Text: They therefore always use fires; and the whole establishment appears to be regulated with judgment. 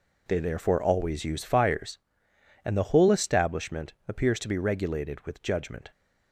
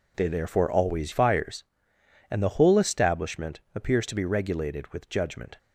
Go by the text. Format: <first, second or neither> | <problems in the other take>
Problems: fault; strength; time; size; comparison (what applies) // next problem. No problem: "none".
first | skips "use"; at 1.1 s